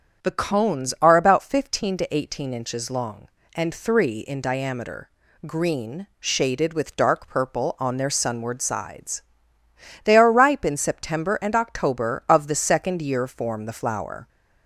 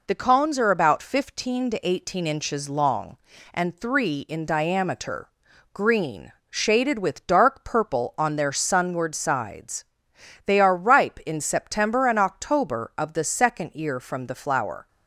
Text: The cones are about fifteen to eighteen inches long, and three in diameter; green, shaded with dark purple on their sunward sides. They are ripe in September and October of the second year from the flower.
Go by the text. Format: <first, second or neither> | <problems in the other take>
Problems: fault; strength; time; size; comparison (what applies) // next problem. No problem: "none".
second | starts louder than the rest; strong; until 1.2 s; 7.5 dB // says "form" for "from"; at 13.2 s